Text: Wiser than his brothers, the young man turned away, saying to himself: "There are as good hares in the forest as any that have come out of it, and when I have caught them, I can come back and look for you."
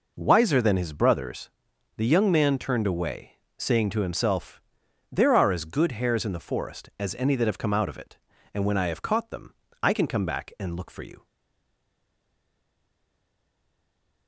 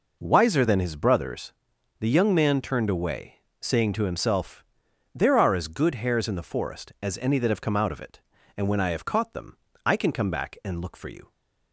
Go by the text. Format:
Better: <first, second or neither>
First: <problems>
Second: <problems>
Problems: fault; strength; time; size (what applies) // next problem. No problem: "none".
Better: second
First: stays silent after the last word; strong; from 11.2 s on; 3.0 s long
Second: none